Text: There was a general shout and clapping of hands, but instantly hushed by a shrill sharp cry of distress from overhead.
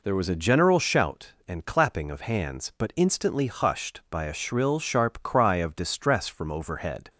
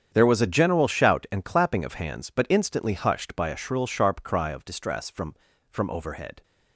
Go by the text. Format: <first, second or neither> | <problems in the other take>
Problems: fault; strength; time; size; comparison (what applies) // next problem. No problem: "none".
first | starts louder than the rest; strong; until 1.1 s; 8.5 dB // says "from" twice; at 5.7 s